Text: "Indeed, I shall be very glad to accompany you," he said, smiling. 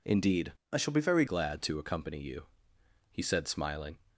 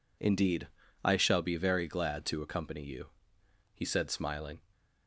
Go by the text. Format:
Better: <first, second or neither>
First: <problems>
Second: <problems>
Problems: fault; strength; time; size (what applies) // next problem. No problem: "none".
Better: second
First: changes voice from "I" to "very"; from 0.7 to 1.2 s; 0.5 s long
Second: none